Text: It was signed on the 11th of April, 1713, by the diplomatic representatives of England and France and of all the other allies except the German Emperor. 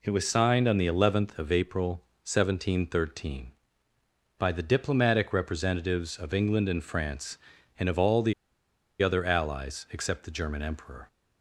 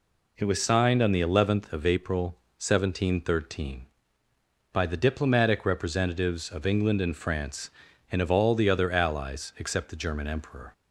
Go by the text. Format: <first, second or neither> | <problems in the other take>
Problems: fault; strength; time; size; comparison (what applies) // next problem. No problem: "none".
second | pauses between "the" and "other"; noticeable; at 8.3 s; 0.67 s long